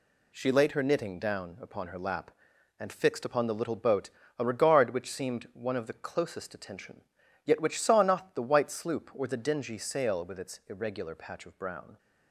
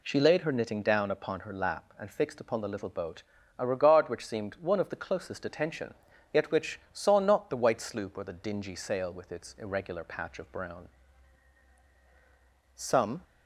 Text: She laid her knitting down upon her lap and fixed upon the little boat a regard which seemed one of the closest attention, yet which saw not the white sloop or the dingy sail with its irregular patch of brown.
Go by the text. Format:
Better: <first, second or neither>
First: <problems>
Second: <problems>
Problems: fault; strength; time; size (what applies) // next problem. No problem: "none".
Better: first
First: pauses between "boat" and "a"; slight; at 4.0 s; 0.30 s long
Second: pauses between "boat" and "a"; slight; at 3.2 s; 0.34 s long // goes on to say "Some"; slight; from 12.7 s on; 0.48 s long